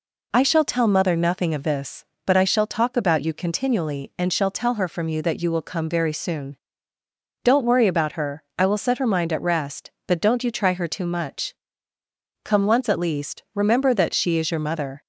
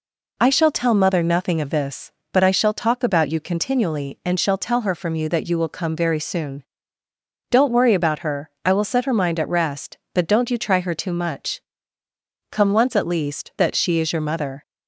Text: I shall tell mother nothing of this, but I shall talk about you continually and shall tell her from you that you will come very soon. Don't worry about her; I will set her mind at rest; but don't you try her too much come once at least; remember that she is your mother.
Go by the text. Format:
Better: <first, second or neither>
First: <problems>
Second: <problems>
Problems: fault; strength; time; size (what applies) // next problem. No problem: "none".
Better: first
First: pauses between "much" and "come"; noticeable; at 11.5 s; 0.90 s long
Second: pauses between "much" and "come"; noticeable; at 11.6 s; 0.90 s long // skips "remember"; at 13.5 s